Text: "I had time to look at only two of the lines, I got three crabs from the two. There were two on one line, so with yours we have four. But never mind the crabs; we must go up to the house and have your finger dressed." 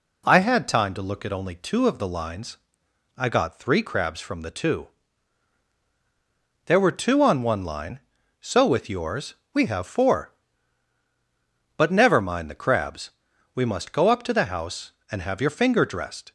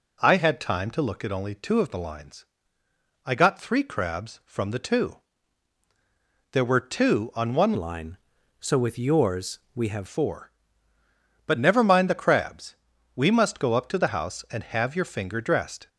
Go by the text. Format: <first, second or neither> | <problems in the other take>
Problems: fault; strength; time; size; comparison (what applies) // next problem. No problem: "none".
first | changes voice from "line" to "have"; from 7.7 to 10.0 s; 2.3 s long // pauses between "yours" and "we"; slight; at 9.5 s; 0.16 s long; slight in the first